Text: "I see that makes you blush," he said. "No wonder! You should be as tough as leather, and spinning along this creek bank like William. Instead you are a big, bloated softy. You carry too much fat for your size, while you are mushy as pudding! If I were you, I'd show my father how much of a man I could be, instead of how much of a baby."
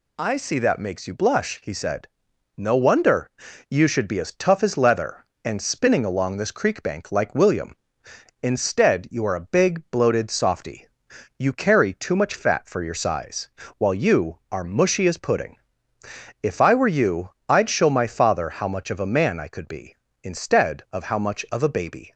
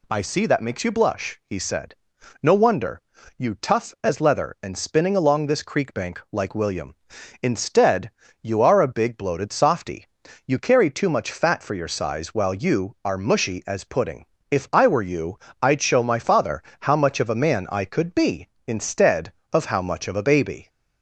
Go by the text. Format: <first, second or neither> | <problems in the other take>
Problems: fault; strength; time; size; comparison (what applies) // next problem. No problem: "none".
first | skips "should be as"; at 3.5 s // pauses between "Instead" and "you"; slight; at 8.1 s; 0.32 s long // pauses between "father" and "how"; slight; at 16.6 s; 0.20 s long